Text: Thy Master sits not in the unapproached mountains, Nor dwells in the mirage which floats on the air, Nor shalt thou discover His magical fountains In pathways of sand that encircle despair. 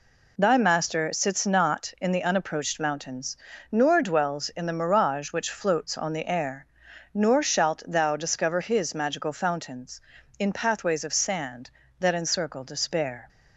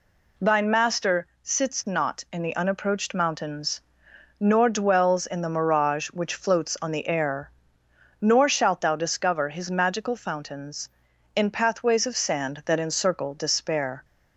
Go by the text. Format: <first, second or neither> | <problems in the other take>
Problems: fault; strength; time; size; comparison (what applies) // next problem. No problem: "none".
first | says "Thine" for "Thy"; at 0.3 s // pauses between "Master" and "sits"; slight; at 1.2 s; 0.18 s long